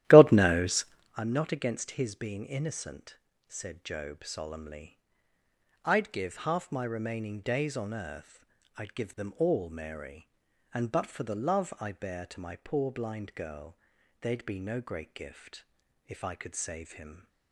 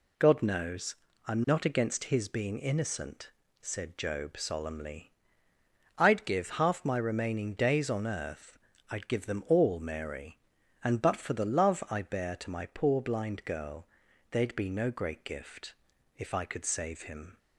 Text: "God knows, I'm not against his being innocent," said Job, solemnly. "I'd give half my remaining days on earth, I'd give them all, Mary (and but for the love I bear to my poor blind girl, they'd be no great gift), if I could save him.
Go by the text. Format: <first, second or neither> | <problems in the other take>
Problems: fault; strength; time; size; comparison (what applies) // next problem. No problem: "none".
second | starts louder than the rest; strong; until 1.3 s; 13.5 dB